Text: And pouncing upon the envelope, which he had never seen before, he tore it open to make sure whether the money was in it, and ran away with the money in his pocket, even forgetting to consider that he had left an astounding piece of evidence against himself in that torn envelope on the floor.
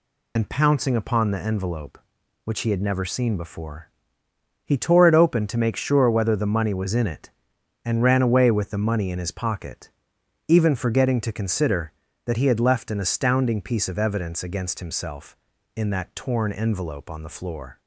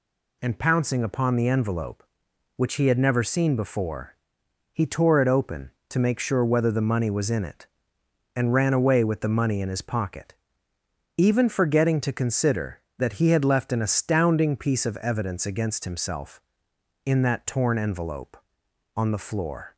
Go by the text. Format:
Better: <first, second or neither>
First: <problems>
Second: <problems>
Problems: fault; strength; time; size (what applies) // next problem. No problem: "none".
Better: second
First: loses the start of "And"; at 0.3 s; 55 ms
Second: none